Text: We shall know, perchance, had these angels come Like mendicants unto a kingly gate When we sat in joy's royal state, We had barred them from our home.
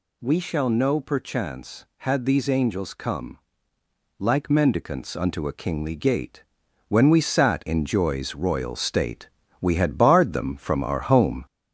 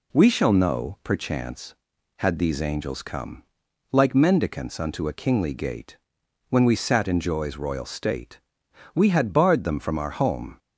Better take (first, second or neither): second